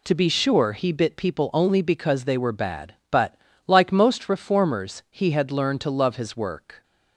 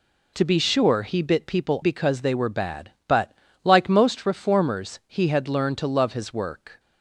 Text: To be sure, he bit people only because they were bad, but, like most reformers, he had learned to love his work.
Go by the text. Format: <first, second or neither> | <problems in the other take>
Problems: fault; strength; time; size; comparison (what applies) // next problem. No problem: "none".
first | skips "only"; at 1.8 s